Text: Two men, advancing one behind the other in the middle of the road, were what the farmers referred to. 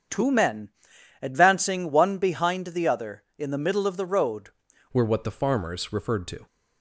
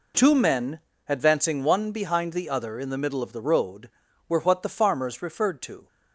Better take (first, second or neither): second